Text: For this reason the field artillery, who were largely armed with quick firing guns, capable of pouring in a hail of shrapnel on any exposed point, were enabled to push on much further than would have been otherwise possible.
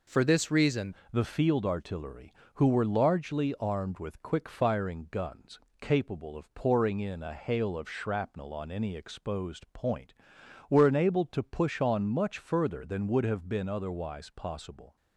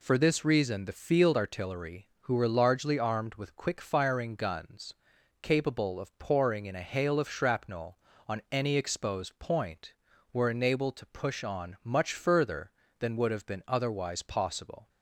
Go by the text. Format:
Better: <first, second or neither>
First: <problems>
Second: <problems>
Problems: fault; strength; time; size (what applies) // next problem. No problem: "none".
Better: second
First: changes voice at "the"; from 1.1 s on; 13.8 s long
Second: none